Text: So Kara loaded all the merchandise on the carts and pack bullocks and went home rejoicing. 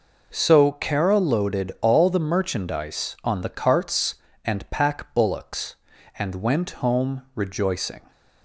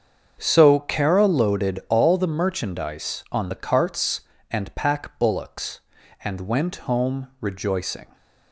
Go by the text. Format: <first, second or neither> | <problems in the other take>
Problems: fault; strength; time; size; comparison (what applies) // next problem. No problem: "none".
first | starts louder than the rest; strong; until 2.0 s; 7.5 dB